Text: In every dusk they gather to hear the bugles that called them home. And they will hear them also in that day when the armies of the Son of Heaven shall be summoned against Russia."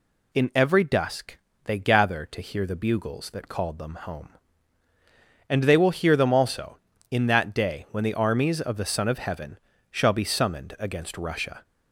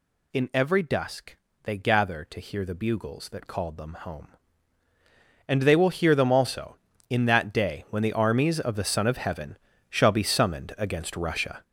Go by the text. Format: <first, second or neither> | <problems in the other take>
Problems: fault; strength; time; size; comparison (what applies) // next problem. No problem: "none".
first | gets louder; strong; throughout; 7.5 dB // pauses between "dusk" and "they"; slight; at 1.3 s; 0.26 s long; slight in the first // pauses between "Heaven" and "shall"; slight; at 9.5 s; 0.32 s long; slight in the first